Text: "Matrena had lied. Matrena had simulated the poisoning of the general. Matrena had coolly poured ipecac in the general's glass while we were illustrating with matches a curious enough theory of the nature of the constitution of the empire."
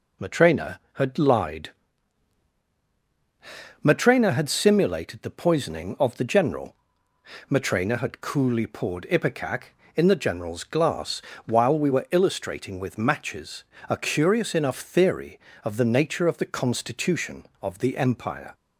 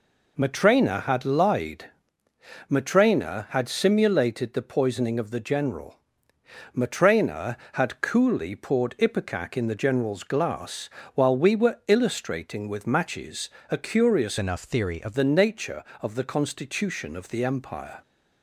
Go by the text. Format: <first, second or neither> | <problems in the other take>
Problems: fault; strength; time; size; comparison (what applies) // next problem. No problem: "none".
first | pauses between "glass" and "while"; slight; at 10.8 s; 0.26 s long; slight in the first // pauses between "matches" and "a"; slight; at 13.4 s; 0.20 s long; slight in the first // changes voice from "enough" to "of"; from 14.3 to 15.1 s; 0.8 s long